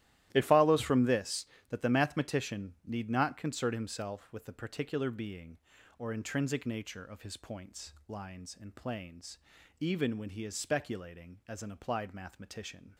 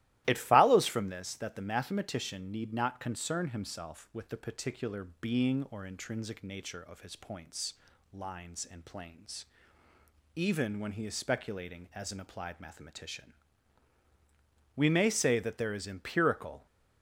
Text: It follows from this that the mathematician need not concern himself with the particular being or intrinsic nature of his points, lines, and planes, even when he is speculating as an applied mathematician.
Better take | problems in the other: first | starts louder than the rest; strong; until 1.2 s; 15.5 dB; strong in the first // pauses between "particular" and "being"; slight; at 5.0 s; 0.16 s long // goes on to say "We may say that there is empirical"; strong; from 14.7 s on; 1.9 s long

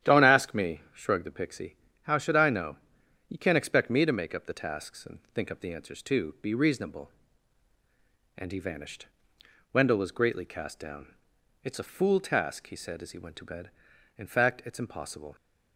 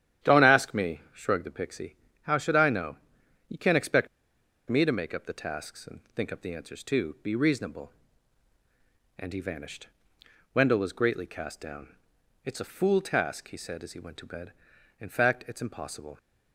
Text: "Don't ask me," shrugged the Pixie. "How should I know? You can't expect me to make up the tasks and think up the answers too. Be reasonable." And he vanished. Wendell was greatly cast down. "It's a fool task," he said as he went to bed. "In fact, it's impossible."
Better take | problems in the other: first | starts louder than the rest; strong; until 1.3 s; 10.5 dB; strong in the first // pauses between "expect" and "me"; noticeable; at 4.0 s; 0.61 s long

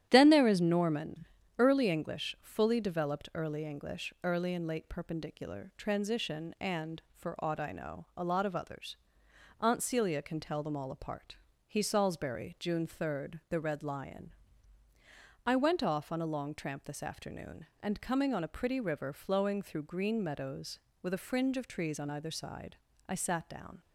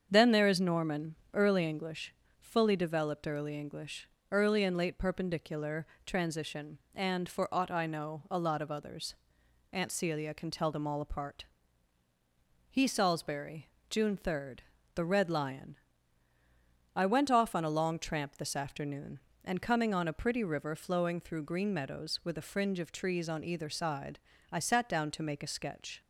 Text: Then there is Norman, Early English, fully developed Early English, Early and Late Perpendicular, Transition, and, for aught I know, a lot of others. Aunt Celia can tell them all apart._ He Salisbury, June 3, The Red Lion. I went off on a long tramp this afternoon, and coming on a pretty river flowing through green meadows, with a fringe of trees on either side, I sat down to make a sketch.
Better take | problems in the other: second | starts louder than the rest; strong; until 1.1 s; 11.5 dB; strong in the second // stops before "to make a sketch"; at 23.8 s

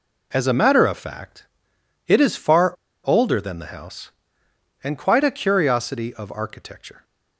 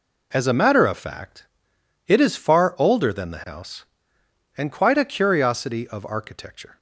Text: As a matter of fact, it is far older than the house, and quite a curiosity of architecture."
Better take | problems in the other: second | pauses between "far" and "older"; slight; at 2.7 s; 0.32 s long

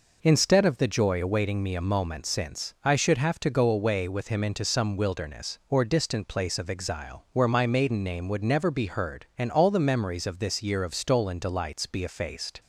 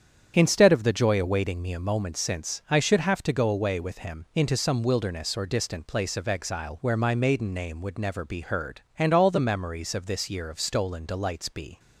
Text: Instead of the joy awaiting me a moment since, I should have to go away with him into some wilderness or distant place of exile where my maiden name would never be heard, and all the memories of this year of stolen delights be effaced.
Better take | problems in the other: first | starts louder than the rest; strong; until 1.3 s; 8.5 dB // stops before "effaced"; at 11.7 s

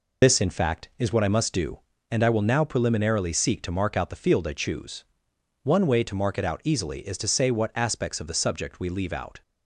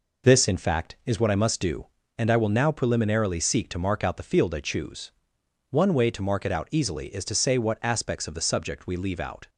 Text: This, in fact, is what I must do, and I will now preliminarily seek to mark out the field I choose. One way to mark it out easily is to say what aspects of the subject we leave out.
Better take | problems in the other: second | loses the start of "This"; at 0.2 s; 55 ms

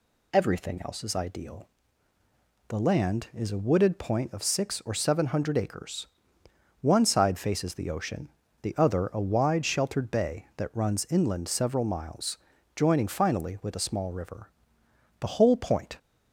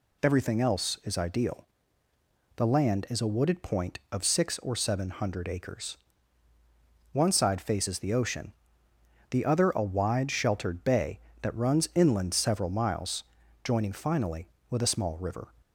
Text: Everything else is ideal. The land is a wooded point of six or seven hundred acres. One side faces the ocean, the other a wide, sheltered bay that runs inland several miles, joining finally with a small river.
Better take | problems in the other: second | goes on to say "The whole point"; noticeable; from 15.1 s on; 0.78 s long

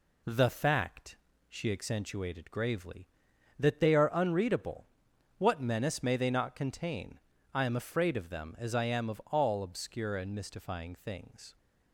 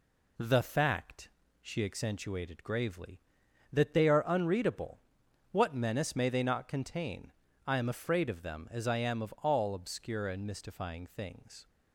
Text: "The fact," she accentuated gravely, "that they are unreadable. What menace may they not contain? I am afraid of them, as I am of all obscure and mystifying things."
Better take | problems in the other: neither | none

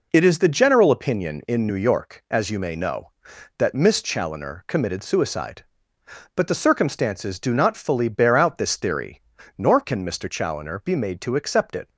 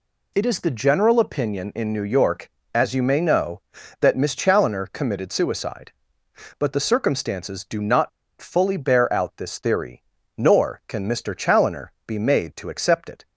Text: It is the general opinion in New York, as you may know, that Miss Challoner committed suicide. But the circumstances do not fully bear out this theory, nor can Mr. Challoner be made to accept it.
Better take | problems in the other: first | pauses between "not" and "fully"; slight; at 8.0 s; 0.31 s long // pauses between "Challoner" and "be"; slight; at 11.9 s; 0.16 s long

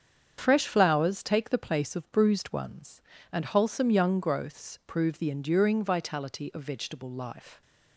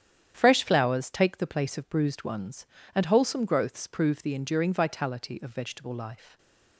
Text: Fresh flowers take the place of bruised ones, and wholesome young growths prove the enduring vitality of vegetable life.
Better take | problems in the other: first | starts louder than the rest; strong; until 1.3 s; 9.5 dB; strong in the first // skips "young"; at 3.4 s

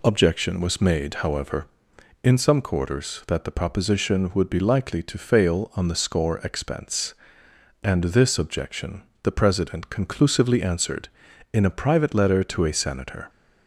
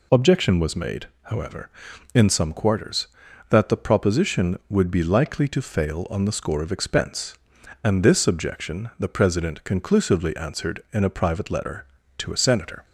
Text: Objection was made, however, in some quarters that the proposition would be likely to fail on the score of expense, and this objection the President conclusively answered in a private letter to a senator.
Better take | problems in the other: second | skips "of"; at 6.3 s // pauses between "objection" and "the"; slight; at 9.0 s; 0.20 s long

